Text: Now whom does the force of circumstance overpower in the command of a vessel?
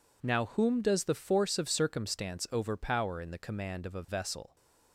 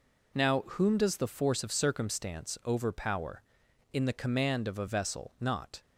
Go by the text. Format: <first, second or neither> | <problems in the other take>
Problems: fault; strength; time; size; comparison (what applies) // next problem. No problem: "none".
first | goes on to say "not"; slight; from 5.4 s on; 0.40 s long